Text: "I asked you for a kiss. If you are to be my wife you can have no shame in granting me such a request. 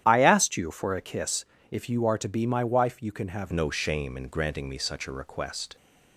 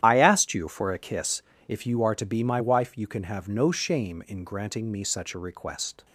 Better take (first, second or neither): second